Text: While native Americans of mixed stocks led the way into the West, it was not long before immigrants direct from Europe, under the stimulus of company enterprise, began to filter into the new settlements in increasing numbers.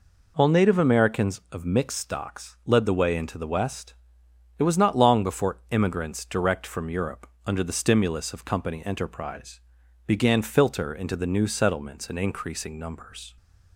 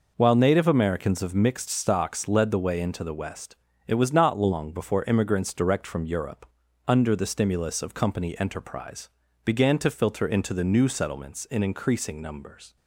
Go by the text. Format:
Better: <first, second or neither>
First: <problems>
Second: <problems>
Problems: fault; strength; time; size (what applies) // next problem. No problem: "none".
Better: second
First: skips "to"; at 10.4 s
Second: none